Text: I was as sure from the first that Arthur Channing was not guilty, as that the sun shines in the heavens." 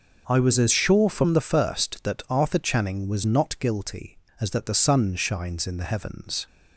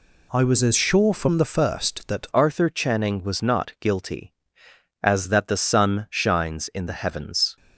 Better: first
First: none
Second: changes voice at "Arthur"; from 2.3 s on; 5.2 s long

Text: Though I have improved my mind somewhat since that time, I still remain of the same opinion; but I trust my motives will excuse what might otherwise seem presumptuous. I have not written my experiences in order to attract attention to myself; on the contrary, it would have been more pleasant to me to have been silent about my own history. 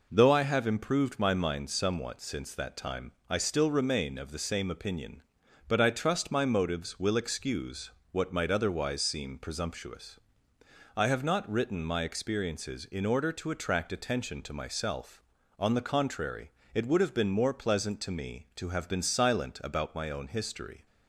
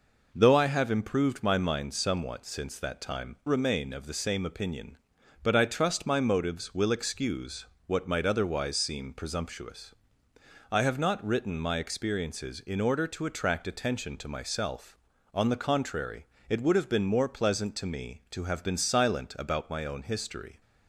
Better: first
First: pauses between "excuse" and "what"; slight; at 7.8 s; 0.22 s long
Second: skips "I still"; at 3.4 s // pauses between "excuse" and "what"; slight; at 7.6 s; 0.22 s long

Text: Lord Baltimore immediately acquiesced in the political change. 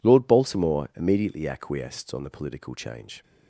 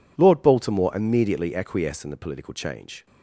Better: second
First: says "on" for "in"; at 2.1 s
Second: none

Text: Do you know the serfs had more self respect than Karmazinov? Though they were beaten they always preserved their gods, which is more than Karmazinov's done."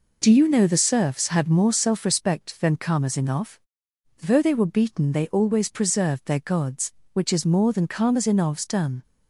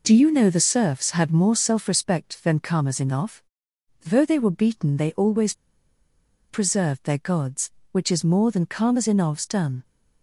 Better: first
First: none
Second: pauses between "always" and "preserved"; noticeable; at 5.5 s; 0.96 s long

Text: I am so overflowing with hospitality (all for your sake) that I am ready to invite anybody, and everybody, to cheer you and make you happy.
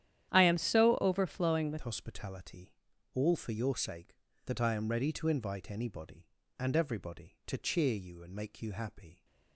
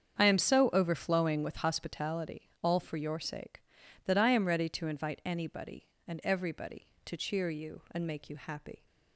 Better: second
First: starts louder than the rest; strong; until 1.3 s; 11 dB // changes voice at "hospitality"; from 1.8 s on; 7.4 s long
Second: starts louder than the rest; strong; until 1.2 s; 7.5 dB

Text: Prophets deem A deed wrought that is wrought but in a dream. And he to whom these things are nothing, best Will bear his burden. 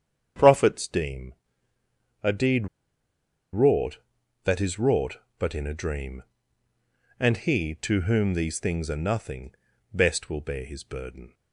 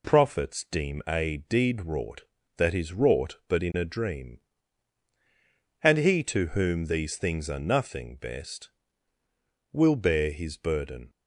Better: second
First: starts louder than the rest; strong; until 2.2 s; 8 dB // pauses between "deem" and "A"; noticeable; at 1.3 s; 0.90 s long // pauses between "deed" and "wrought"; noticeable; at 2.6 s; 0.85 s long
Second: none

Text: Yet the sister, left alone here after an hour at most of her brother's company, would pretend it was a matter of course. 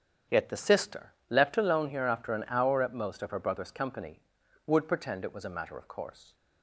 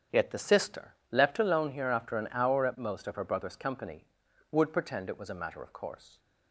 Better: neither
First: starts louder than the rest; strong; until 1.4 s; 8.5 dB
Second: starts louder than the rest; strong; until 1.3 s; 8.5 dB

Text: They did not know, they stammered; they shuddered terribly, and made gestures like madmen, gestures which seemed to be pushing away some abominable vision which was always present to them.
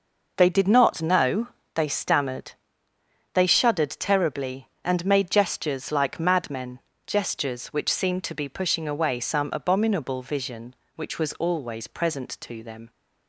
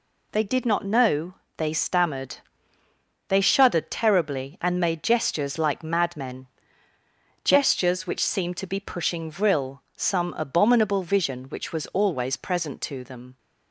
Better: first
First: none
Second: says "vril" for "away"; at 9.3 s

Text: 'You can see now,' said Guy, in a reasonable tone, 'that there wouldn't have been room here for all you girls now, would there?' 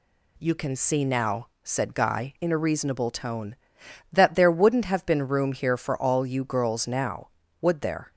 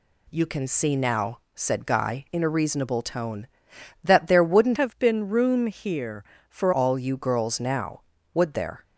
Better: first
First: none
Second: changes voice from "have" to "for"; from 4.7 to 6.7 s; 2.0 s long

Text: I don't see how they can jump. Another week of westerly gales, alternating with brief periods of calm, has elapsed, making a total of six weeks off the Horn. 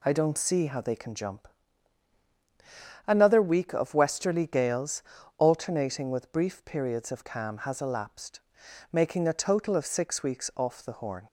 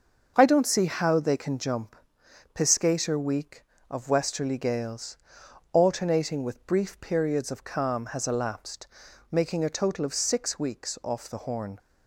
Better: first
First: none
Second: starts louder than the rest; until 1.3 s; 6.5 dB // says "Piscator" for "Another"; at 2.5 s

